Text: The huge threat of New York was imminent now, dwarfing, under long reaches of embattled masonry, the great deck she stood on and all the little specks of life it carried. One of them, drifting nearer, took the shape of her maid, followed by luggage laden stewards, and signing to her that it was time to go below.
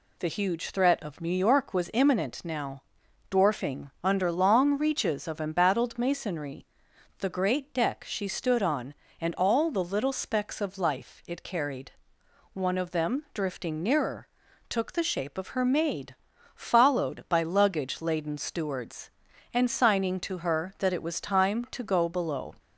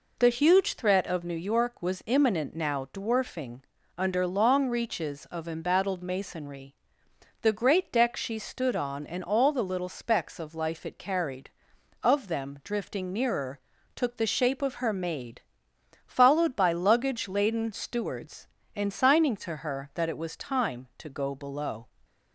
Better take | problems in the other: first | skips "One"; at 11.7 s

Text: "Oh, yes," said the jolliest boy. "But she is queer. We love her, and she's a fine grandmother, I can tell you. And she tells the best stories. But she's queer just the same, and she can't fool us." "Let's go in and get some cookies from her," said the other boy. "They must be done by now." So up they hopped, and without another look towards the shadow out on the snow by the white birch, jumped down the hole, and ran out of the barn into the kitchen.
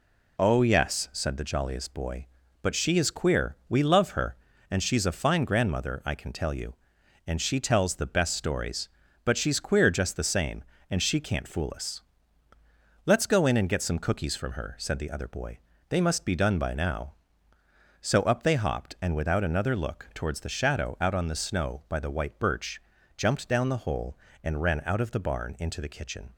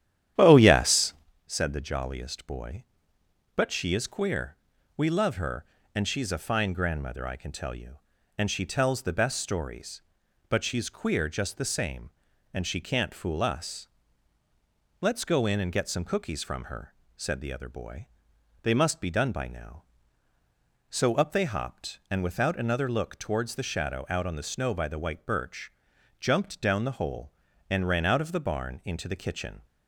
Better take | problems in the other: first | starts louder than the rest; strong; until 1.3 s; 11 dB

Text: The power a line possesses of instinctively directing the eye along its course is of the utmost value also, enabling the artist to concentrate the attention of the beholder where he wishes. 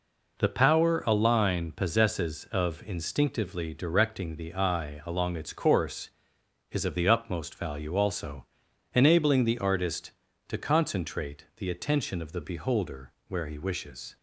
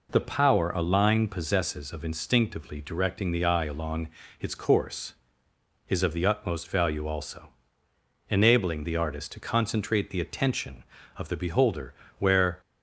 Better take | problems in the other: first | pauses between "along" and "its"; slight; at 4.0 s; 0.32 s long // pauses between "beholder" and "where"; slight; at 11.9 s; 0.24 s long; slight in the first // stops before "he wishes"; at 12.6 s

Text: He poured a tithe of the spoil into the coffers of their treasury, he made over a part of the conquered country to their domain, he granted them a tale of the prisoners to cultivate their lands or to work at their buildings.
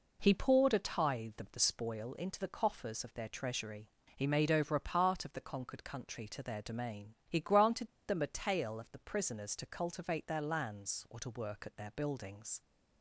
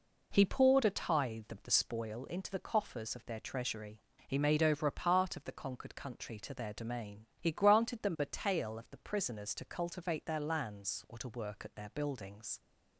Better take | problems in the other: second | pauses between "granted" and "them"; slight; at 7.8 s; 0.18 s long

